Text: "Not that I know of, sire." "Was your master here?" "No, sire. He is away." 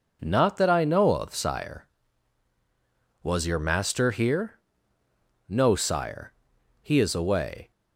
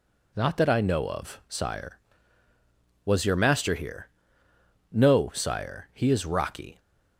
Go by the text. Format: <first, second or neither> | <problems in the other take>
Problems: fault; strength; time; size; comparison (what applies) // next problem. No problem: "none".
first | says "rocky" for "away"; at 6.2 s